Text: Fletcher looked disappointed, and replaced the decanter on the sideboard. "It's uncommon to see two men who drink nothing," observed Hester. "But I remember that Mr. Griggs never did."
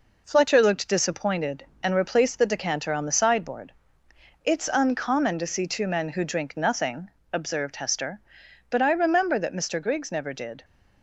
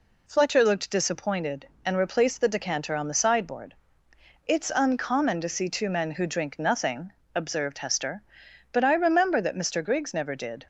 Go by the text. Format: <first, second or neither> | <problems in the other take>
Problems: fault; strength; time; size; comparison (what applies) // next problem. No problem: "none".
second | gets quieter; throughout; 3.5 dB